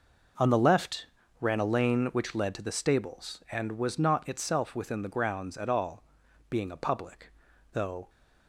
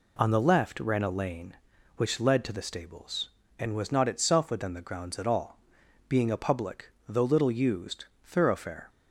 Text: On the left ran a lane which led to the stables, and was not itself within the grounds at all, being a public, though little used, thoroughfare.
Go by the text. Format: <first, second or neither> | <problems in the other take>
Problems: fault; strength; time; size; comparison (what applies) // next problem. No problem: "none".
second | pauses between "left" and "ran"; slight; at 1.0 s; 0.34 s long // stops before "little used thoroughfare"; at 8.0 s